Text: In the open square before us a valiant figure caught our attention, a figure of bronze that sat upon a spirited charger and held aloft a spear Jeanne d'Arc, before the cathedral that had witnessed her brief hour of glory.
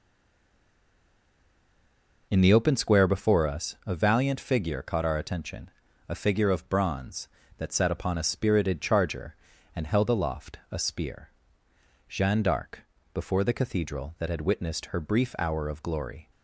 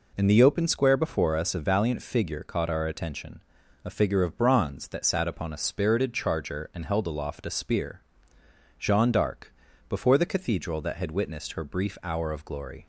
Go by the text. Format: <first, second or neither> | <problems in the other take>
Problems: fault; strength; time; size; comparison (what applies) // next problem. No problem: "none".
second | stays silent before the first word; until 2.3 s; 2.3 s long // pauses between "spear" and "Jeanne"; noticeable; at 11.2 s; 0.80 s long; noticeable in the second